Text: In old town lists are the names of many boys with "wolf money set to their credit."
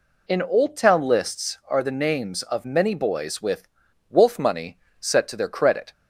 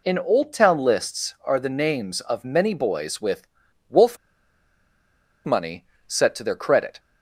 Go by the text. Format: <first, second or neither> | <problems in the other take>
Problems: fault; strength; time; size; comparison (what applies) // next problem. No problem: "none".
first | pauses between "with" and "wolf"; at 3.4 s; 0.42 s long; also in the first // pauses between "wolf" and "money"; strong; at 4.1 s; 1.2 s long // pauses between "money" and "set"; slight; at 5.8 s; 0.22 s long; slight in the first